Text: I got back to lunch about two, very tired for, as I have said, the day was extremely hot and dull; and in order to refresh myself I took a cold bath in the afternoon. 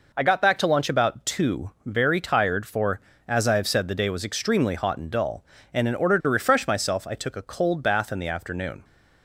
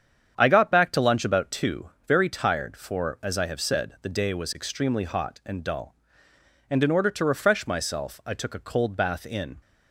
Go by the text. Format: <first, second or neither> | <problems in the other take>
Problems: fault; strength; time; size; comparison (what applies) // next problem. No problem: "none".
first | starts louder than the rest; strong; until 1.3 s; 8.5 dB // stops before "the afternoon"; at 9.6 s